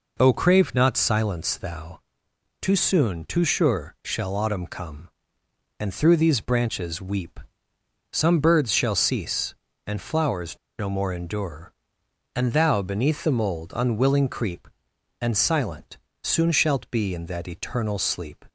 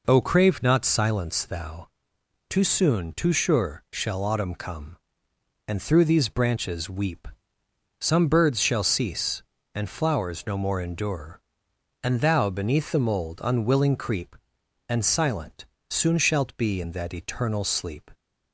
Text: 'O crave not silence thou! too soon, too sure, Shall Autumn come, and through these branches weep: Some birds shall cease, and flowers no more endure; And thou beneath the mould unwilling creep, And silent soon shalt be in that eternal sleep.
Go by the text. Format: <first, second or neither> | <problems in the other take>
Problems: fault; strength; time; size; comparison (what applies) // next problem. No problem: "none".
second | pauses between "flowers" and "no"; slight; at 10.5 s; 0.20 s long // pauses between "silent" and "soon"; slight; at 15.9 s; 0.24 s long; slight in the second